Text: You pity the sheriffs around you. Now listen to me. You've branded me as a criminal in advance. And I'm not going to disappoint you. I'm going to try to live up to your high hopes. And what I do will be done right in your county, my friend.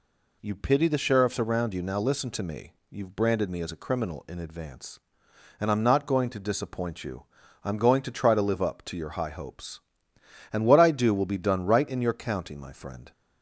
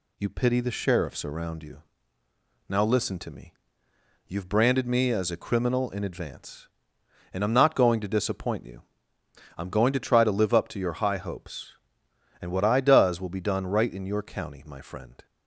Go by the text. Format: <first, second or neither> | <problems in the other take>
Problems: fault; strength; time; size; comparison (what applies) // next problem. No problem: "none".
first | says "does" for "do"; at 12.7 s